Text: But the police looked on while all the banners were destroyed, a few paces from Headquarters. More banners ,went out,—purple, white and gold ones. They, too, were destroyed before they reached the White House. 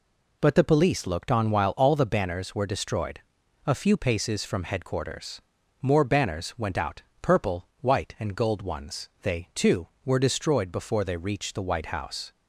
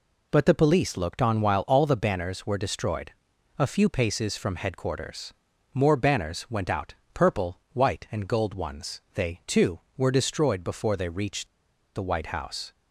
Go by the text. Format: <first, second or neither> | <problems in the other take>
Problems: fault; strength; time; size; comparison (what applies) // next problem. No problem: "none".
first | pauses between "reached" and "the"; noticeable; at 11.4 s; 0.48 s long